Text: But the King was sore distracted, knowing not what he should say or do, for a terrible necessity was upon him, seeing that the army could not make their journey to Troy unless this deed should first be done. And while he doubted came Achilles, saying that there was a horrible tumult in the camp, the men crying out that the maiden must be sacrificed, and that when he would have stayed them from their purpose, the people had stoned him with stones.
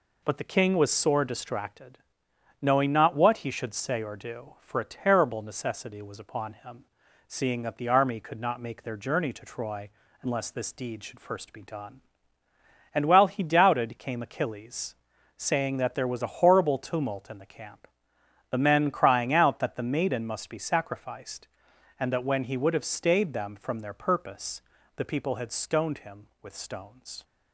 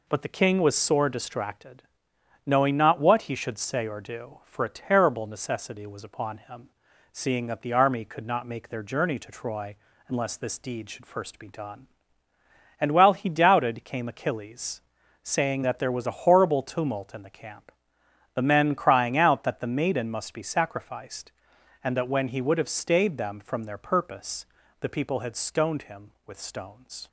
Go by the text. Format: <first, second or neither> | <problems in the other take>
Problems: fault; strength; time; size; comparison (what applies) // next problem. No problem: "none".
neither | pauses between "Troy" and "unless"; slight; the same in both